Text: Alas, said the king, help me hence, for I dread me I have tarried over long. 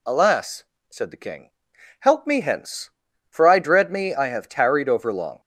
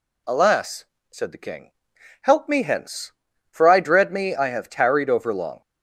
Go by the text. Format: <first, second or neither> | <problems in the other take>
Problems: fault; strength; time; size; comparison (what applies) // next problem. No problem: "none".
neither | none